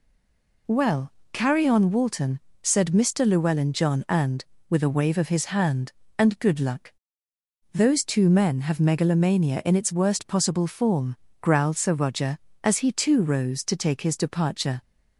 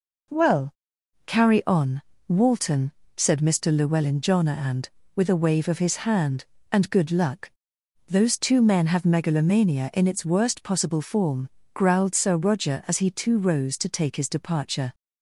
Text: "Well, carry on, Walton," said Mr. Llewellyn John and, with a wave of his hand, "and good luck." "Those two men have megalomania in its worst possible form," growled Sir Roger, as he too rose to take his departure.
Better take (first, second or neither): second